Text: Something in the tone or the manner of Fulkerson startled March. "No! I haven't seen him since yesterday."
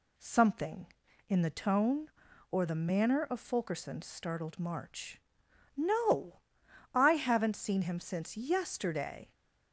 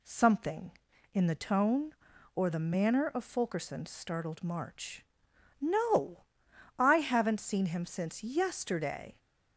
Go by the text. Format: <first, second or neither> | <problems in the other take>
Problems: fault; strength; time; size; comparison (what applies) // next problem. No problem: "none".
neither | none